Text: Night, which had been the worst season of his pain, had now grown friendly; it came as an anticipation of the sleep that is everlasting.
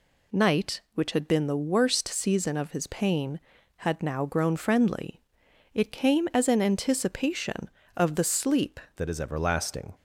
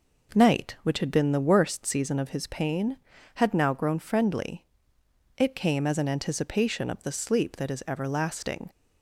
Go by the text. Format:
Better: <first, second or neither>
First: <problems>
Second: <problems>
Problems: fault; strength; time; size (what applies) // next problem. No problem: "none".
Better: second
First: changes voice at "that"; from 8.9 s on; 1.0 s long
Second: none